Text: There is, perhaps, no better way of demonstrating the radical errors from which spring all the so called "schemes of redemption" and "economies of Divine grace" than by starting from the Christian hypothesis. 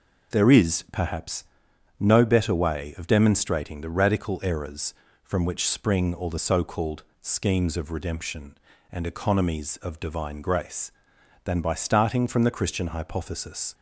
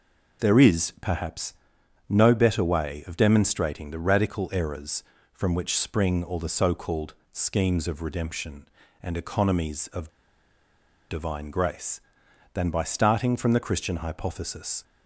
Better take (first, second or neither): first